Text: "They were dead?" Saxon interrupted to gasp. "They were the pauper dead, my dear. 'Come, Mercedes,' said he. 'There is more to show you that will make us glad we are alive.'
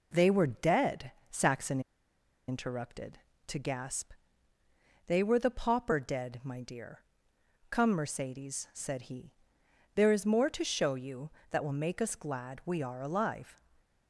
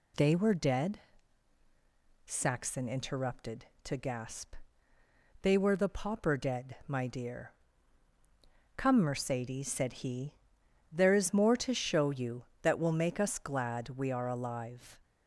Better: second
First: pauses between "Saxon" and "interrupted"; noticeable; at 1.8 s; 0.67 s long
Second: none

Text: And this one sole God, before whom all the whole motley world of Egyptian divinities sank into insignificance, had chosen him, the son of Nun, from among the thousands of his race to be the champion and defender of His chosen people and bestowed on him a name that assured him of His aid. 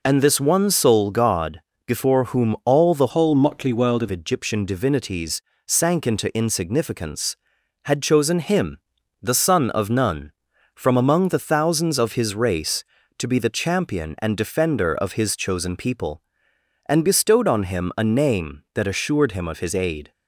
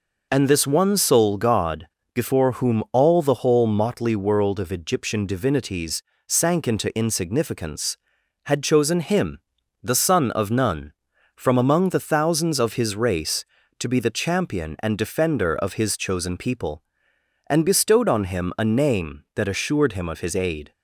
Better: second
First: changes voice from "whole" to "of"; from 3.0 to 4.0 s; 1.0 s long // pauses between "divinities" and "sank"; slight; at 5.4 s; 0.26 s long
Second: pauses between "divinities" and "sank"; slight; at 6.0 s; 0.26 s long

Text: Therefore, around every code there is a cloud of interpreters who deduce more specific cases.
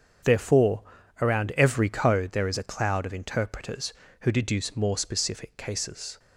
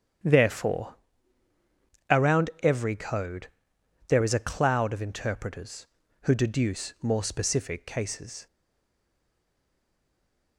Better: first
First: starts louder than the rest; strong; until 1.6 s; 8 dB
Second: starts louder than the rest; strong; until 2.3 s; 9 dB // pauses between "code" and "there"; noticeable; at 3.4 s; 0.62 s long // stays silent after the last word; from 8.4 s on; 2.1 s long

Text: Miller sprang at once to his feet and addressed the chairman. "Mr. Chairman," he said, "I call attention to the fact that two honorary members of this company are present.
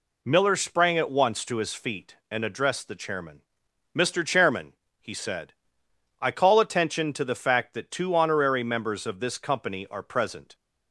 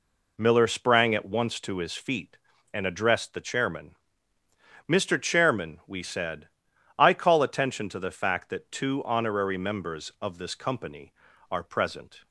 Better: first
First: none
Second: says "we" for "he"; at 5.8 s

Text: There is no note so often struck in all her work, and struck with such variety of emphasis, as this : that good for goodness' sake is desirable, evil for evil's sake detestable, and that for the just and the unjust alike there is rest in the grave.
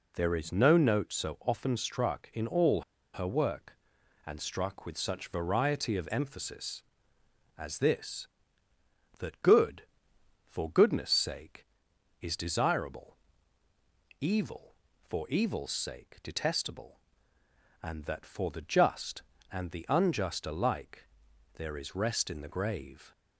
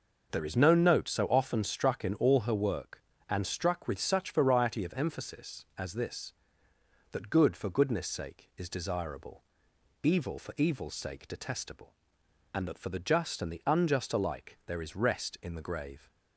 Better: second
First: pauses between "all" and "her"; slight; at 2.8 s; 0.32 s long // pauses between "alike" and "there"; noticeable; at 21.0 s; 0.46 s long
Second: none

